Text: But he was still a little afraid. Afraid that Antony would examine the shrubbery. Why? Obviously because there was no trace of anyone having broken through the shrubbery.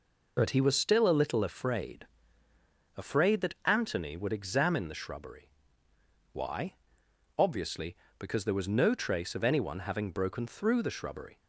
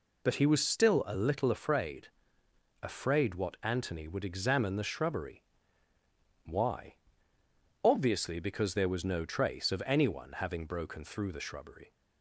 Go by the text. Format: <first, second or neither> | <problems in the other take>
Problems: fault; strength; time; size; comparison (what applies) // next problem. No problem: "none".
first | says "what" for "that"; at 3.3 s